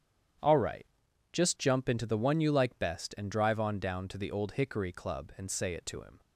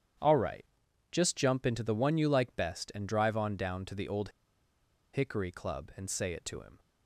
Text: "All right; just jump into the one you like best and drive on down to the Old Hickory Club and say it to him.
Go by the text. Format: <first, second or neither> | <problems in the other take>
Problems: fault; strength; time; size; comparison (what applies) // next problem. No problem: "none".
first | starts louder than the rest; strong; until 1.6 s; 9.5 dB; strong in the first // pauses between "Old" and "Hickory"; noticeable; at 4.2 s; 0.84 s long